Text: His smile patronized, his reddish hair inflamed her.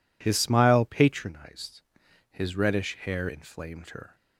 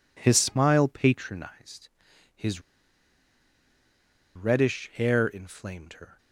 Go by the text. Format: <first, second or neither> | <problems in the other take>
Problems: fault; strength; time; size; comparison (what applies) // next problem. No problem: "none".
first | pauses between "his" and "reddish"; strong; at 2.5 s; 1.7 s long